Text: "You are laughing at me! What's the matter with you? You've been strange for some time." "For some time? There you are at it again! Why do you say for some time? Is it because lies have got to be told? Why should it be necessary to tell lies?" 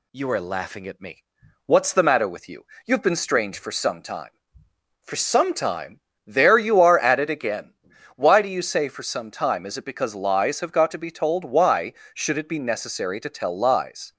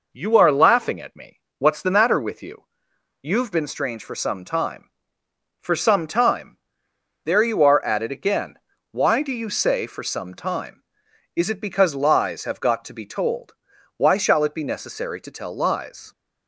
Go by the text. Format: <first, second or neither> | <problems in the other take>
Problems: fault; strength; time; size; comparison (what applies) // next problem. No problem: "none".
first | says "shall" for "should"; at 14.1 s